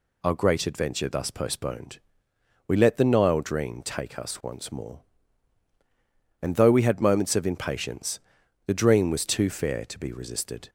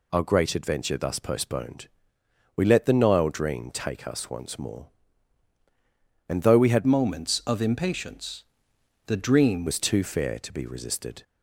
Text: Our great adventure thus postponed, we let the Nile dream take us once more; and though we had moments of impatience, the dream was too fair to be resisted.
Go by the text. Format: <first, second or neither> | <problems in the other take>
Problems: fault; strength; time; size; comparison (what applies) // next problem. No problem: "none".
first | changes voice from "moments" to "dream"; from 6.8 to 9.6 s; 2.8 s long